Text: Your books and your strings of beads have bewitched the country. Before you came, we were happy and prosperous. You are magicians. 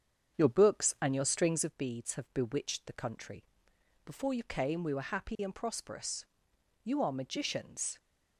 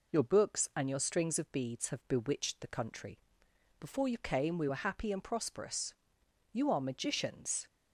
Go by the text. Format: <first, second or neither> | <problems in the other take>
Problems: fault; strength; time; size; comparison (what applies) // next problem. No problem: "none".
second | starts louder than the rest; strong; until 1.7 s; 7.5 dB